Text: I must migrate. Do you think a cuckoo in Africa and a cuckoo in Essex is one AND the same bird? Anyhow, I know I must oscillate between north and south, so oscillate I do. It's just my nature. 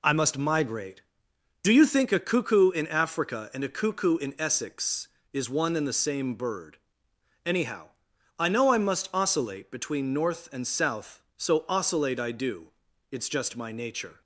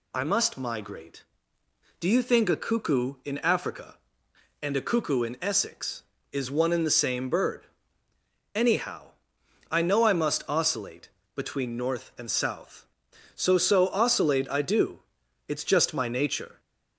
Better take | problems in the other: first | pauses between "oscillate" and "between"; slight; at 11.0 s; 0.26 s long // says "so" twice; at 13.5 s

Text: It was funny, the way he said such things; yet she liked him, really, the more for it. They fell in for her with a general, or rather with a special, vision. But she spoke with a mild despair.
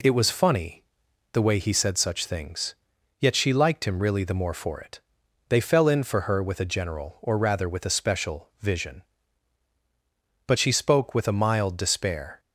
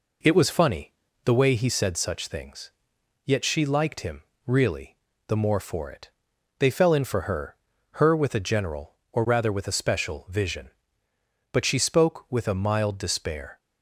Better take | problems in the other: first | says "her" twice; at 7.9 s

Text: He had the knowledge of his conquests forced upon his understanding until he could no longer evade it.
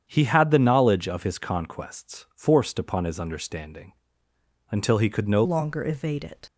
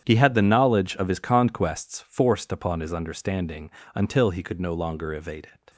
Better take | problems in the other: second | starts louder than the rest; strong; until 1.0 s; 8.5 dB; strong in the second // pauses between "understanding" and "until"; noticeable; at 3.9 s; 0.80 s long; slight in the second // changes voice at "longer"; from 5.4 s on; 1.0 s long

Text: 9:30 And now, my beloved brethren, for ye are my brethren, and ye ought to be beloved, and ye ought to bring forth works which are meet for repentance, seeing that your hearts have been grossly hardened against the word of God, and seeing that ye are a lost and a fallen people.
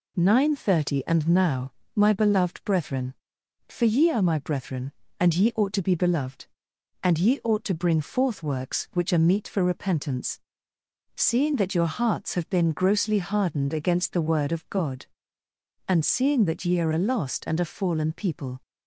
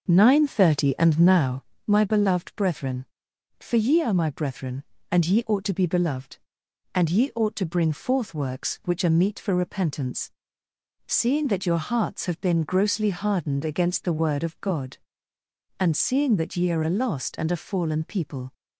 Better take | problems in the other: first | starts louder than the rest; noticeable; until 1.7 s; 6 dB

